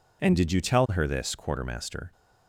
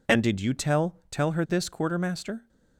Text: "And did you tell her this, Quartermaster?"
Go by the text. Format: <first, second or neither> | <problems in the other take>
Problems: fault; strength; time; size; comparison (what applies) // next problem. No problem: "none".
first | says "tell" twice; at 1.0 s